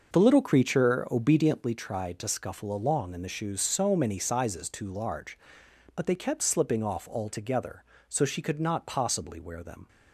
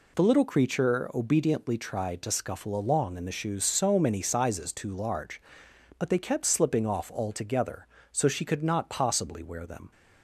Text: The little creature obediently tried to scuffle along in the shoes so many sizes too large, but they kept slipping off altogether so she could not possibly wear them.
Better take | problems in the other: second | starts louder than the rest; noticeable; until 1.7 s; 6 dB

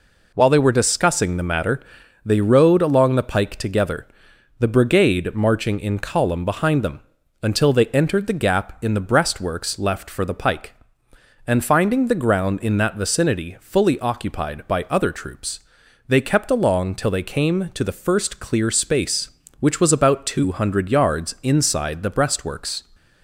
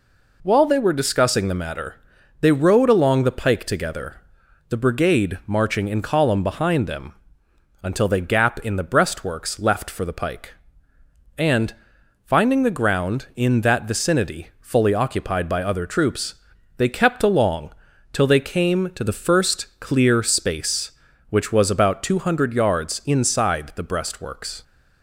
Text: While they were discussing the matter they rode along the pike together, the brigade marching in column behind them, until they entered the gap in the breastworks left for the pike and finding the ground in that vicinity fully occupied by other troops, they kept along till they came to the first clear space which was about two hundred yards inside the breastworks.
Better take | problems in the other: first | pauses between "matter" and "they"; at 1.9 s; 0.44 s long; noticeable in the first // skips "entered the"; at 8.2 s // pauses between "and" and "finding"; noticeable; at 11.7 s; 0.50 s long // pauses between "along" and "till"; at 17.7 s; 0.40 s long

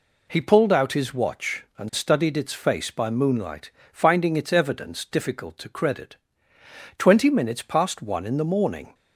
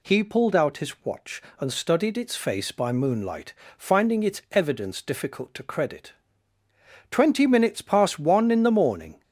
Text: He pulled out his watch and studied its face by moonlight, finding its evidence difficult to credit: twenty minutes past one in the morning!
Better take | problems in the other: neither | none

